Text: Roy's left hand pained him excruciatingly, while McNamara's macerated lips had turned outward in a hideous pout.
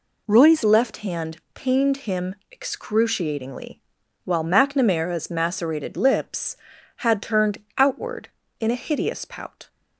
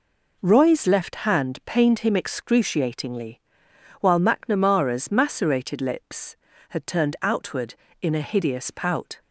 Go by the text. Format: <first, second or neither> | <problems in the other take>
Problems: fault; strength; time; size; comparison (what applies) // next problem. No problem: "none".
second | changes voice at "left"; from 0.6 s on; 9.0 s long // pauses between "hand" and "pained"; slight; at 1.3 s; 0.16 s long // pauses between "him" and "excruciatingly"; slight; at 2.3 s; 0.16 s long // pauses between "turned" and "outward"; slight; at 7.5 s; 0.18 s long